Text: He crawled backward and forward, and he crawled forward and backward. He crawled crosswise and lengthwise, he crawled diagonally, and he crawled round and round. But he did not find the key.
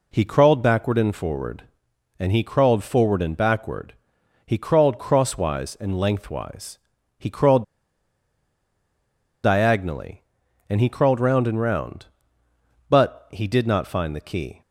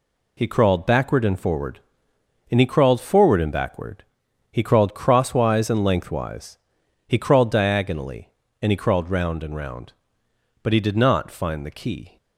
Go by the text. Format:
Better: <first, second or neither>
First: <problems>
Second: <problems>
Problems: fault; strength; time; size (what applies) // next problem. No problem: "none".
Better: second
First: pauses between "crawled" and "diagonally"; strong; at 7.6 s; 1.7 s long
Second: none